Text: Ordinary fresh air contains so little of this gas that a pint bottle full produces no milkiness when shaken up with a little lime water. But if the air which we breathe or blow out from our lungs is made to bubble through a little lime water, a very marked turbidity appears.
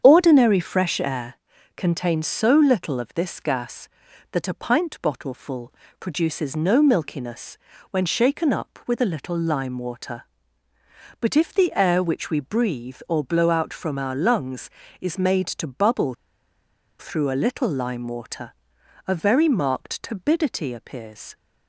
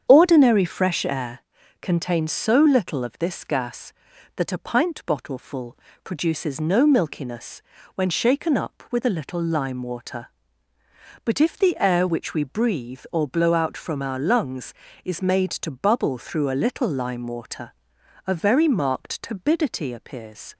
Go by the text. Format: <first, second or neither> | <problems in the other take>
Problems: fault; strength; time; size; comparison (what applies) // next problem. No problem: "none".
second | starts louder than the rest; strong; until 1.0 s; 8 dB; strong in the second // pauses between "air" and "contains"; at 1.3 s; 0.42 s long; also in the second // pauses between "full" and "produces"; slight; at 5.7 s; 0.28 s long; slight in the second // pauses between "milkiness" and "when"; slight; at 7.5 s; 0.36 s long; slight in the second // pauses between "bubble" and "through"; noticeable; at 16.1 s; 0.84 s long